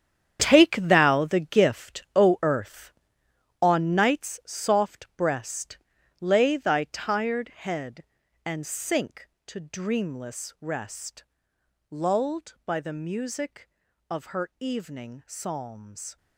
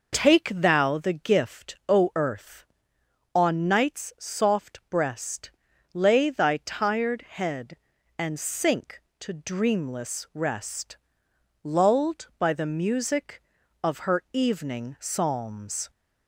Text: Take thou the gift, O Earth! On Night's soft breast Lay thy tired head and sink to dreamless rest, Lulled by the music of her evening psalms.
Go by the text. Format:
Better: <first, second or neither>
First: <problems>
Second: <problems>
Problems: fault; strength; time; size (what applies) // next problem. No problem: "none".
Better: second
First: gets quieter; strong; throughout; 13 dB // pauses between "breast" and "Lay"; at 5.7 s; 0.42 s long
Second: pauses between "breast" and "Lay"; at 5.4 s; 0.42 s long